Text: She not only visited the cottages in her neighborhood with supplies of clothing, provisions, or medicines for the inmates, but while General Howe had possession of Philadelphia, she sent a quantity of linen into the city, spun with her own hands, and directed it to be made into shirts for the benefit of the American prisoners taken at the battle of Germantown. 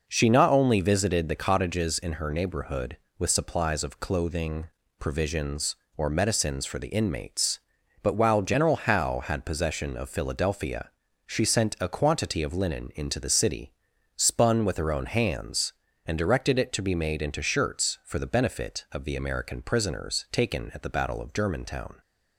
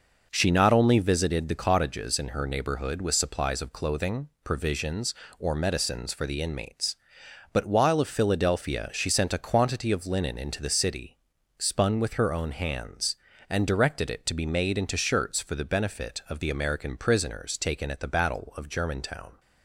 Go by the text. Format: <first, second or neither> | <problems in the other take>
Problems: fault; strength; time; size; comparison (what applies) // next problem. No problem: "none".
first | skips "General Howe had possession"; at 7.9 s